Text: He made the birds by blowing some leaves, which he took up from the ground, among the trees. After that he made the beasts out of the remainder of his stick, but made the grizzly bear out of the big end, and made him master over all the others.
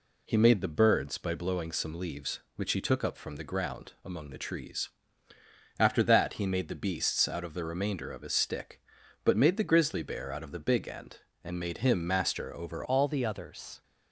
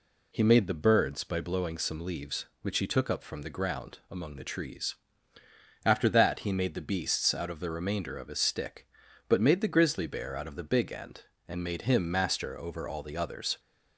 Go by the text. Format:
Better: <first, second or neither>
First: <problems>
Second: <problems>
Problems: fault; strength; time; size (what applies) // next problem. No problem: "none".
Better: second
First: changes voice at "all"; from 12.8 s on; 1.0 s long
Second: none